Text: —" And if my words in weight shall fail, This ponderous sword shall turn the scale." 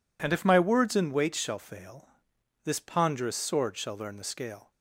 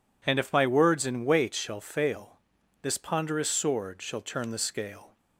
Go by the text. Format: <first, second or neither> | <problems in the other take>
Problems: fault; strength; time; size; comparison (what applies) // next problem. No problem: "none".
second | says "learn" for "turn"; at 3.9 s